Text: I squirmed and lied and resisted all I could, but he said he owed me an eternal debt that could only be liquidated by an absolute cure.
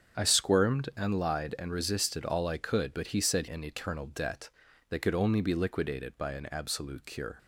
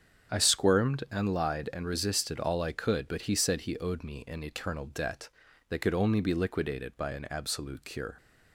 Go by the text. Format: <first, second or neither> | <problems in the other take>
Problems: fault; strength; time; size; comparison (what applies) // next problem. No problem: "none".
second | starts louder than the rest; strong; until 1.2 s; 7.5 dB; strong in the second // skips "he owed me"; at 3.4 s